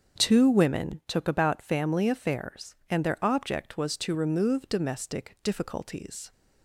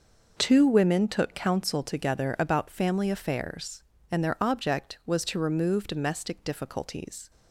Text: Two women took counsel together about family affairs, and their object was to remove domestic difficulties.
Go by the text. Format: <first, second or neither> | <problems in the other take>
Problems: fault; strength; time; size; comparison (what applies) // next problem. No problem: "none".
second | starts louder than the rest; until 1.2 s; 7 dB // skips "counsel together"; at 1.2 s